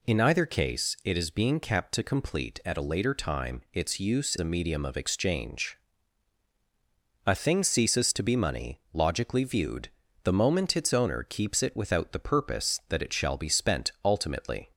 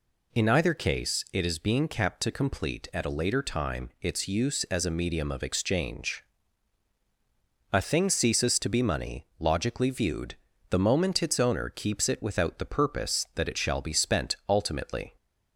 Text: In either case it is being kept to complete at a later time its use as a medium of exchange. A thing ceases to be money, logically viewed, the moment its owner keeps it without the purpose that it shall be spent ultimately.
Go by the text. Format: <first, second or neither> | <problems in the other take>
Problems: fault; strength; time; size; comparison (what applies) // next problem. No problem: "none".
second | skips "as"; at 4.3 s